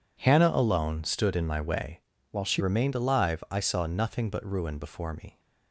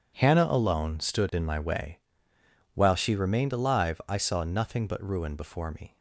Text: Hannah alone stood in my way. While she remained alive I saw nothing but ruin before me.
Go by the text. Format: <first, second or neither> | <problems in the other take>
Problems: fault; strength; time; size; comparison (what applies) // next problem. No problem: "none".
second | changes voice from "While" to "she"; from 2.2 to 2.6 s; 0.4 s long